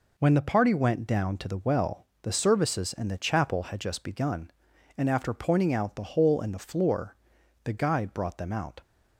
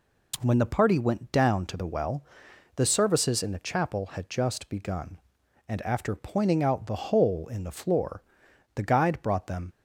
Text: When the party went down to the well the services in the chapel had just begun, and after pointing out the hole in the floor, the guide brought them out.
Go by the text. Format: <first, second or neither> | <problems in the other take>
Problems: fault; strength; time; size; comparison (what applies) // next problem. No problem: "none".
first | pauses between "well" and "the"; noticeable; at 2.2 s; 0.52 s long; slight in the first // stops before "out"; at 9.7 s